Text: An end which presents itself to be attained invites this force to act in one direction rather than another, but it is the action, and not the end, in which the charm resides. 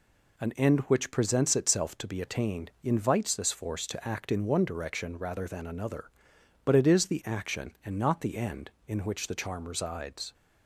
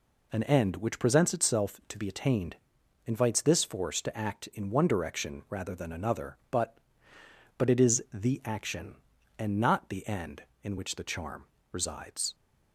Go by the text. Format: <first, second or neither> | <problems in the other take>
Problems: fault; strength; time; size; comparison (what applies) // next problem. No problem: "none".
first | pauses between "attained" and "invites"; noticeable; at 2.5 s; 0.50 s long // says "but" twice; at 7.5 s // pauses between "charm" and "resides"; slight; at 11.4 s; 0.26 s long